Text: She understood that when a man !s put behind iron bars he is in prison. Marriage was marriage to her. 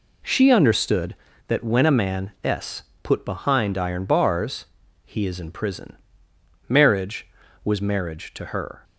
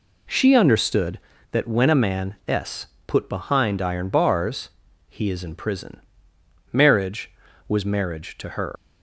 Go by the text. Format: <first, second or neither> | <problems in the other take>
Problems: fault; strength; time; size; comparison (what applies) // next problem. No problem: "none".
first | pauses between "s" and "put"; slight; at 2.8 s; 0.20 s long; slight in the first // pauses between "bars" and "he"; at 4.6 s; 0.42 s long; also in the first // leaves "her" unfinished; at 8.7 s; 120 ms